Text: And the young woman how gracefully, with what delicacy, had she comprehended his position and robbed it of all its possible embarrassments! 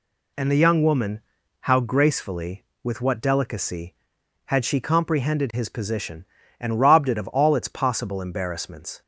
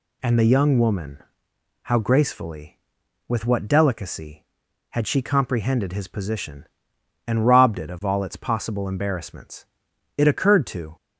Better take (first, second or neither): first